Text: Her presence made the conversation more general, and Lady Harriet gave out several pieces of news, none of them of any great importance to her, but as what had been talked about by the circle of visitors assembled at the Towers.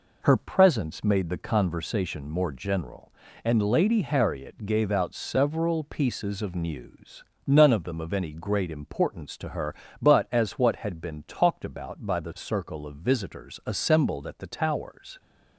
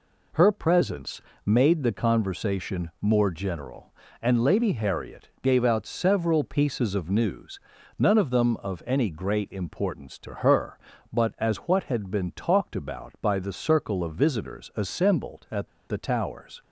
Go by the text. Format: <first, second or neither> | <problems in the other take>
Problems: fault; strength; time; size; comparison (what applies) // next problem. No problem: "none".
first | pauses between "presence" and "made"; slight; at 1.1 s; 0.24 s long // pauses between "at" and "the"; slight; at 15.6 s; 0.20 s long